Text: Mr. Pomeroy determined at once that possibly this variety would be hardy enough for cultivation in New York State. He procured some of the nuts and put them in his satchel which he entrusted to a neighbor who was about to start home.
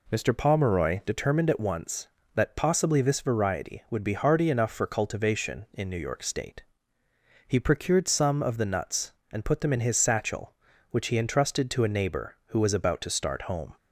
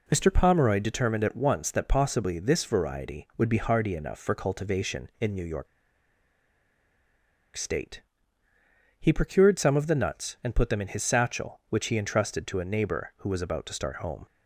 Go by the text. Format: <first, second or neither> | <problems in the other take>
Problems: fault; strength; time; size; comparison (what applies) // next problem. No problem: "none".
first | pauses between "York" and "State"; strong; at 5.6 s; 1.8 s long